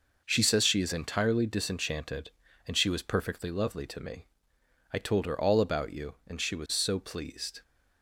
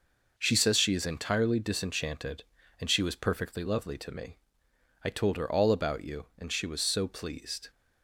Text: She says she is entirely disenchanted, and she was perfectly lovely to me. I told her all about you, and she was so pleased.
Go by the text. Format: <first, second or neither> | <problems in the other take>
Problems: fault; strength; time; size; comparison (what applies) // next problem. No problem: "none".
neither | none